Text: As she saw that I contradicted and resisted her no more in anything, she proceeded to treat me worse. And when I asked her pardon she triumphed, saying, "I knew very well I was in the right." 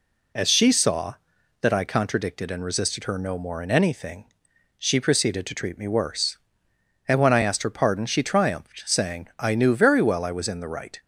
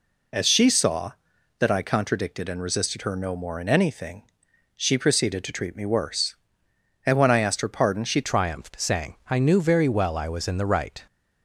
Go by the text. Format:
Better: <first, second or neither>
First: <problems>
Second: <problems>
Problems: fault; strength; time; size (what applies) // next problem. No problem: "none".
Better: first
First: none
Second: changes voice at "triumphed"; from 8.2 s on; 2.8 s long